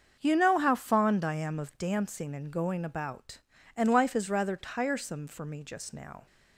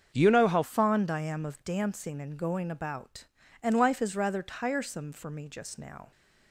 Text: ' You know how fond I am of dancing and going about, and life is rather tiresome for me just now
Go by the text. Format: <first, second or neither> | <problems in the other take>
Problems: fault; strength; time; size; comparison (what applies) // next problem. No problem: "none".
first | starts louder than the rest; until 1.1 s; 7 dB; also in the first // changes voice from "You" to "how"; from 0.1 to 0.6 s; 0.5 s long